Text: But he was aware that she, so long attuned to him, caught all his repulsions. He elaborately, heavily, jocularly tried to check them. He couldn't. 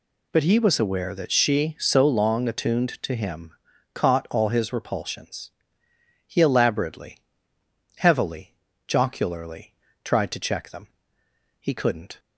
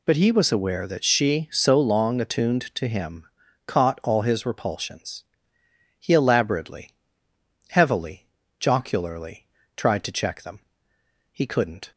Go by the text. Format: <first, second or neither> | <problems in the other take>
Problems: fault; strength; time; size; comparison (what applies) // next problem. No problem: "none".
neither | pauses between "jocularly" and "tried"; slight; the same in both